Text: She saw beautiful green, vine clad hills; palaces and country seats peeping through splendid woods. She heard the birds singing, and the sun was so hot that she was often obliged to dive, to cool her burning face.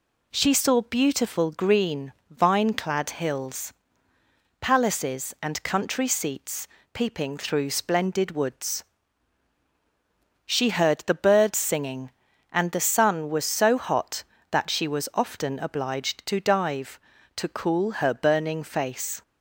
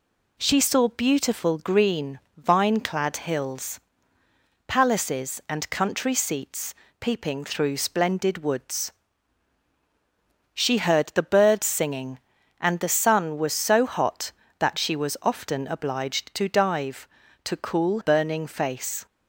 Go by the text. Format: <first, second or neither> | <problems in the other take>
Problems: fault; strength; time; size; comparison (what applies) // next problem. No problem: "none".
first | pauses between "seats" and "peeping"; slight; at 6.7 s; 0.26 s long; slight in the first // skips "her"; at 18.0 s